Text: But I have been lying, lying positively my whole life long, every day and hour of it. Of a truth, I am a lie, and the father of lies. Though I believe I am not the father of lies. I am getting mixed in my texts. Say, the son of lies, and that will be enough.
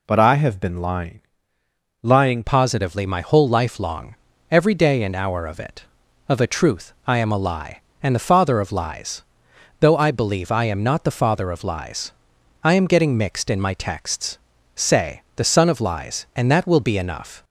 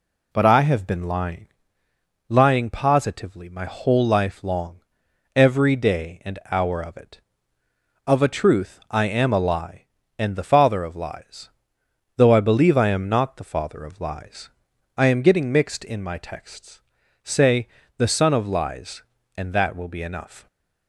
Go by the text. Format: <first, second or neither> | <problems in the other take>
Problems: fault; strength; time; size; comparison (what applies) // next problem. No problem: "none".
second | changes voice at "positively"; from 2.4 s on; 15.0 s long